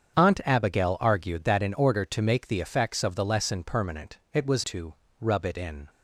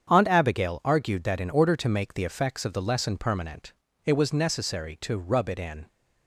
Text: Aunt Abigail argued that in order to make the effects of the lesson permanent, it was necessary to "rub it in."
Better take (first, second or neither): second